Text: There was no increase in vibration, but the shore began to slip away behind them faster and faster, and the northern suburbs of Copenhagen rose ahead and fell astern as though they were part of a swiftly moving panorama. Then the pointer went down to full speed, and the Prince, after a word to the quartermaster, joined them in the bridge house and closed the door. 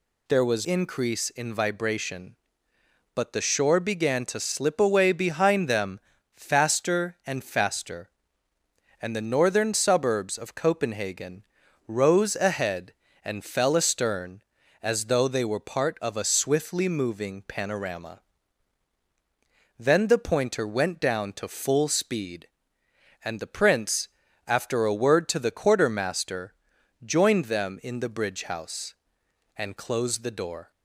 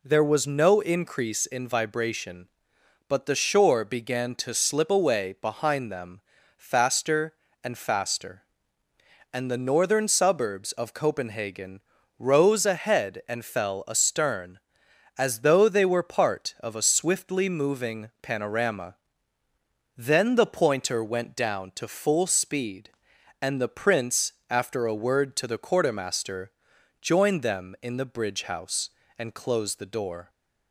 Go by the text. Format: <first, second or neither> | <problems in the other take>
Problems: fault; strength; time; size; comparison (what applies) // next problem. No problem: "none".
second | skips "no"; at 0.6 s // pauses between "them" and "faster"; slight; at 6.0 s; 0.34 s long; slight in the second // pauses between "Copenhagen" and "rose"; at 11.4 s; 0.42 s long; slight in the second